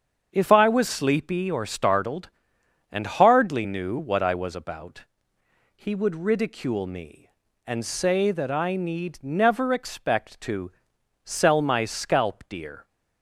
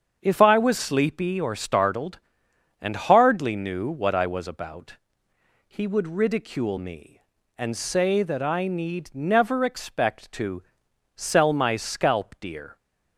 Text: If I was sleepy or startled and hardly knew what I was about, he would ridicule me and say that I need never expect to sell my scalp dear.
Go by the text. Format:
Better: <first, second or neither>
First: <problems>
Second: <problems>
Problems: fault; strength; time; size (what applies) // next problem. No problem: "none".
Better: neither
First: starts louder than the rest; strong; until 1.3 s; 7.5 dB // pauses between "to" and "sell"; noticeable; at 10.7 s; 0.52 s long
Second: starts louder than the rest; strong; until 1.2 s; 7.5 dB // pauses between "to" and "sell"; noticeable; at 10.6 s; 0.52 s long